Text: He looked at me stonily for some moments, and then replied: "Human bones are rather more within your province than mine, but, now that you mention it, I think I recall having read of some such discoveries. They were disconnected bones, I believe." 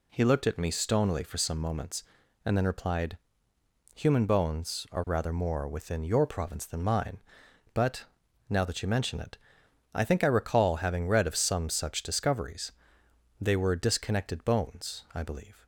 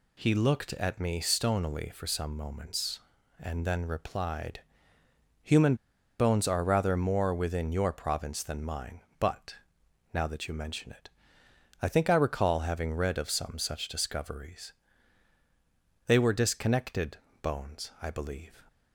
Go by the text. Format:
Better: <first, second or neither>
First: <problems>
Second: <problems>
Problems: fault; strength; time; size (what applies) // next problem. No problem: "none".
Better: first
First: none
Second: pauses between "Human" and "bones"; at 5.7 s; 0.43 s long // pauses between "disconnected" and "bones"; slight; at 17.1 s; 0.24 s long